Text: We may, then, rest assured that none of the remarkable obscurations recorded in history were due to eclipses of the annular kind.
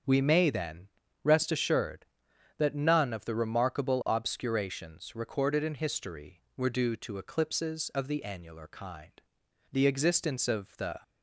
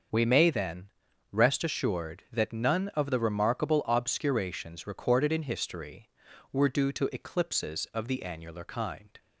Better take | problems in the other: second | starts louder than the rest; until 1.4 s; 7 dB; also in the second // goes on to say "The existence of the"; noticeable; from 9.7 s on; 1.2 s long

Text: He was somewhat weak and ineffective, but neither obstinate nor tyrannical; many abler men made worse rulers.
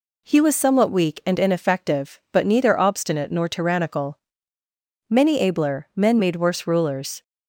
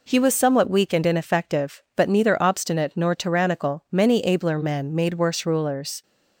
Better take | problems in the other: neither | none

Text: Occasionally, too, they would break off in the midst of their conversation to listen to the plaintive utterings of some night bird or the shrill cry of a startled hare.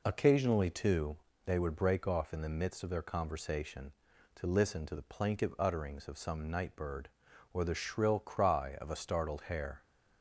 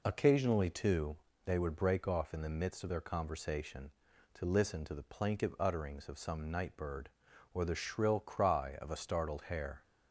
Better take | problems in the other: neither | none

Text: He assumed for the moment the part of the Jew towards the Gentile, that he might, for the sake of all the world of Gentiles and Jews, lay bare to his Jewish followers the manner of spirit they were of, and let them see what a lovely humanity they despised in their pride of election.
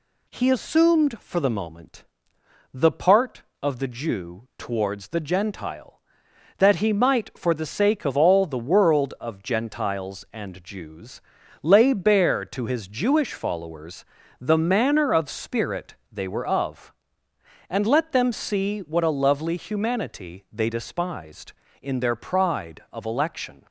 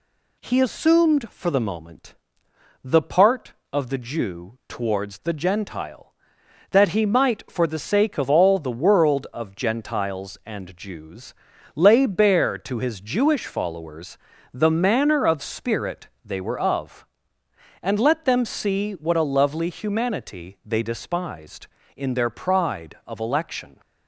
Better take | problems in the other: neither | pauses between "moment" and "the"; noticeable; the same in both // pauses between "followers" and "the"; slight; the same in both // pauses between "spirit" and "they"; slight; the same in both

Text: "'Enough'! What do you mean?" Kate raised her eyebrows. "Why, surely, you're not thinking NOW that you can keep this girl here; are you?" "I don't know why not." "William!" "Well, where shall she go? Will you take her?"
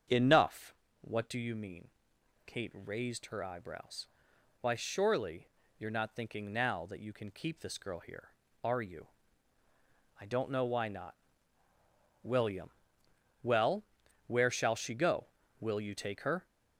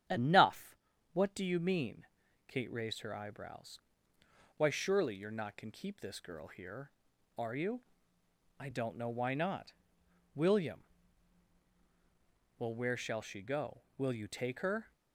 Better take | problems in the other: first | starts louder than the rest; strong; until 1.4 s; 9 dB; strong in the first // skips "thinking NOW that you"; at 5.5 s

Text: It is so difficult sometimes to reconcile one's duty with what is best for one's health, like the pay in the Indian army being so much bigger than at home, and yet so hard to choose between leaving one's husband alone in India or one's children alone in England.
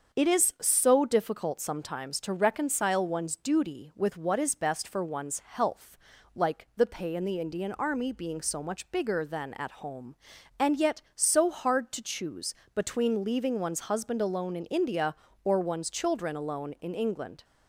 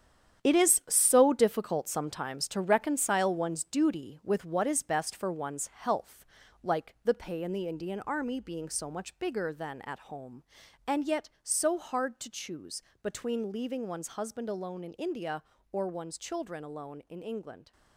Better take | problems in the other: first | gets quieter; strong; throughout; 9 dB // starts louder than the rest; strong; until 1.5 s; 9.5 dB; also in the first // pauses between "choose" and "between"; slight; at 12.8 s; 0.20 s long; slight in the first

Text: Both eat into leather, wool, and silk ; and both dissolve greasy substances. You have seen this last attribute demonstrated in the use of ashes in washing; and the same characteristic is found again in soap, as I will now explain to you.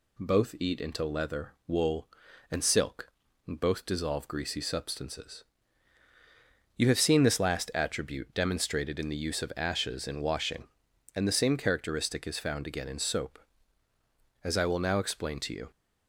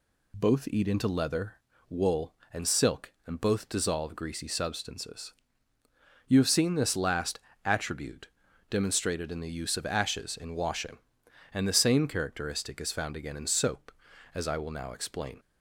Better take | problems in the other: first | pauses between "last" and "attribute"; slight; at 7.3 s; 0.24 s long // pauses between "attribute" and "demonstrated"; at 8.2 s; 0.42 s long // stops before "to you"; at 15.3 s

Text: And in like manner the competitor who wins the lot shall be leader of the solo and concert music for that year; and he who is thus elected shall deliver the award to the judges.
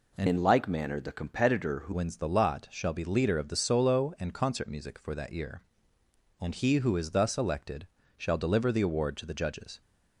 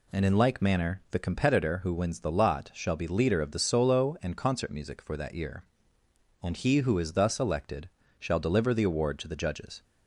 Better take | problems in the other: second | changes voice from "in" to "who"; from 0.2 to 1.9 s; 1.7 s long // pauses between "elected" and "shall"; slight; at 7.8 s; 0.28 s long; slight in the second

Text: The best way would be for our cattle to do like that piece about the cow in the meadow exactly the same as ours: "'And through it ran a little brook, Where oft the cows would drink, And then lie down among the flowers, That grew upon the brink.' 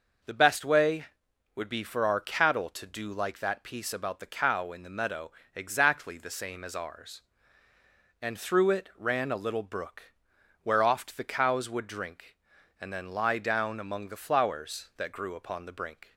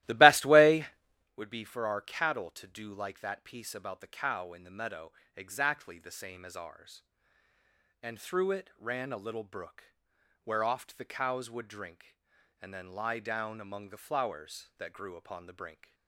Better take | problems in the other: first | starts louder than the rest; strong; until 1.4 s; 16 dB // pauses between "meadow" and "exactly"; slight; at 5.1 s; 0.24 s long; slight in the first

